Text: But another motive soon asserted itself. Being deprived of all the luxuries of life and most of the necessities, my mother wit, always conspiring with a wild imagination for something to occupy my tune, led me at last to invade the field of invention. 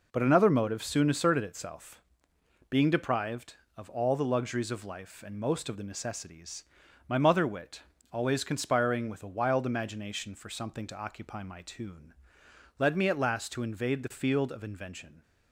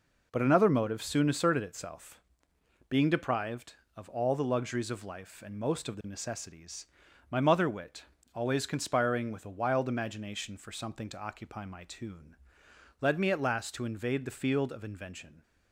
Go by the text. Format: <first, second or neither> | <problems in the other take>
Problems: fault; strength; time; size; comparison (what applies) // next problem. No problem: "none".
neither | none